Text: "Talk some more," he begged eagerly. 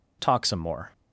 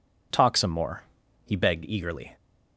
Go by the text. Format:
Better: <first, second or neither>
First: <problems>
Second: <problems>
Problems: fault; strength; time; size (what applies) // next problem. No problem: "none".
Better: second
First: stops before "he begged eagerly"; at 0.9 s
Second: none